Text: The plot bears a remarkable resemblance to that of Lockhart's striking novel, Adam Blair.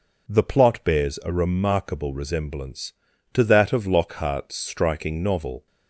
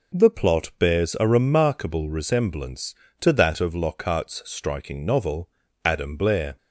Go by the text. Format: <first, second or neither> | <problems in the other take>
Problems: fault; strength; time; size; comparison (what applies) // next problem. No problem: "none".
second | stops before "Adam Blair"; at 5.6 s